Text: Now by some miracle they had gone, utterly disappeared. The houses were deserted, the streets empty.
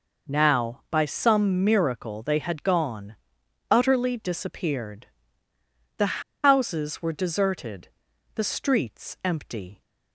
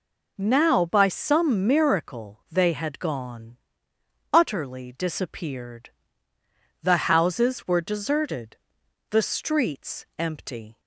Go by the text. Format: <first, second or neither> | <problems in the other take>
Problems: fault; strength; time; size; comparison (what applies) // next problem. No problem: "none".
second | pauses between "The" and "houses"; slight; at 6.2 s; 0.22 s long